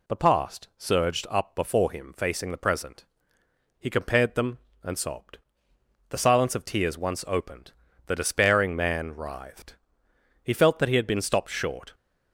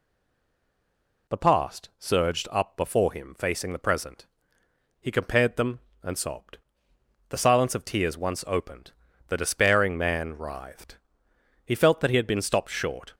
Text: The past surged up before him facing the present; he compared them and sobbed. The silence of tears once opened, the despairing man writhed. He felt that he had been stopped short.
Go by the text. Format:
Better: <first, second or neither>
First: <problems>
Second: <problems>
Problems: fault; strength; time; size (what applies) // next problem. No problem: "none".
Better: first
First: none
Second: stays silent before the first word; noticeable; until 1.2 s; 1.2 s long